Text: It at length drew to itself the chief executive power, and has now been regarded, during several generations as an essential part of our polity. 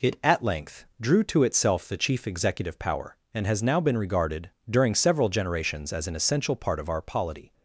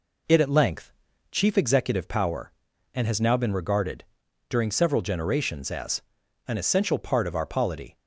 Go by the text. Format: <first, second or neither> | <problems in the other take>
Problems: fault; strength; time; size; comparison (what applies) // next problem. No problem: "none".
first | skips "drew to itself the"; at 1.1 s // pauses between "as" and "an"; noticeable; at 6.0 s; 0.46 s long